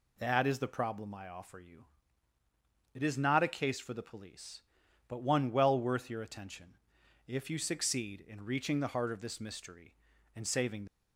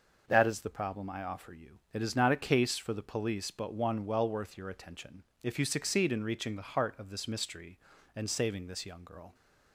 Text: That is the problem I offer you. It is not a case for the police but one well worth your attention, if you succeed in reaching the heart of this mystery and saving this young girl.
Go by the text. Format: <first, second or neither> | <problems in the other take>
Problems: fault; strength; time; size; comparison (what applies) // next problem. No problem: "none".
second | stops before "this young girl"; at 10.8 s